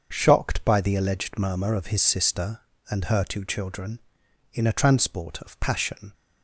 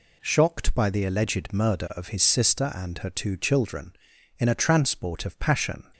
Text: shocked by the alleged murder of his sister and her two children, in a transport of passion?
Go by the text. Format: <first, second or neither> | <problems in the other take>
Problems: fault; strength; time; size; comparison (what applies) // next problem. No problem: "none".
second | starts louder than the rest; until 1.1 s; 6.5 dB // says "murmur" for "murder"; at 1.3 s